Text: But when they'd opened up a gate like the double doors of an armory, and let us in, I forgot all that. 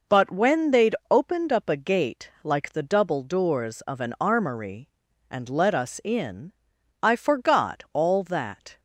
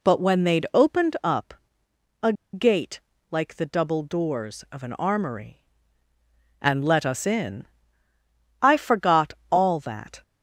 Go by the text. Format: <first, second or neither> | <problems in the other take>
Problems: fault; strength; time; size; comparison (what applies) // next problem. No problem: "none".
first | pauses between "up" and "a"; noticeable; at 1.5 s; 0.70 s long // pauses between "a" and "gate"; slight; at 2.3 s; 0.20 s long // pauses between "gate" and "like"; slight; at 3.0 s; 0.30 s long // pauses between "forgot" and "all"; slight; at 9.3 s; 0.18 s long